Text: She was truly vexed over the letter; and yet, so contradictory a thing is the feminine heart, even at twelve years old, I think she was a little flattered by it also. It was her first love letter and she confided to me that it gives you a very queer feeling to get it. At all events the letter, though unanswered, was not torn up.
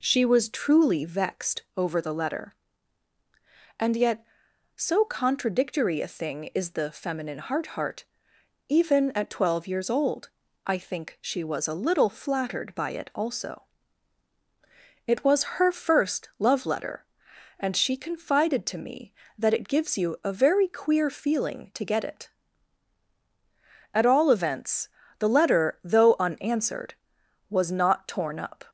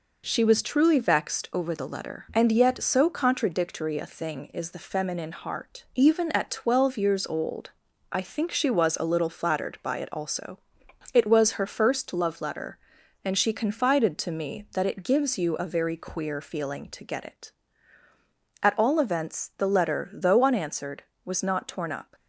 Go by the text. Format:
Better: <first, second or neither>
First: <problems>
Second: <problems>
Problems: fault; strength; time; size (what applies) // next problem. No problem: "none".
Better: second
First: pauses between "vexed" and "over"; slight; at 1.6 s; 0.16 s long // says "heart" twice; at 7.7 s // pauses between "events" and "the"; slight; at 24.8 s; 0.32 s long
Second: none